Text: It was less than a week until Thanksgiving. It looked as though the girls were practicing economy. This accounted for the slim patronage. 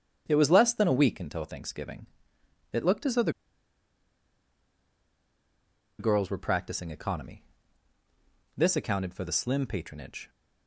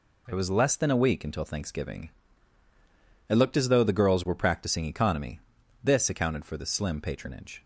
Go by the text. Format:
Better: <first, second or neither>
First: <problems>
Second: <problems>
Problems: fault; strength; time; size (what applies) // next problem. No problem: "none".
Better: second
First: starts louder than the rest; strong; until 1.2 s; 9 dB // pauses between "the" and "girls"; strong; at 3.3 s; 2.6 s long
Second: none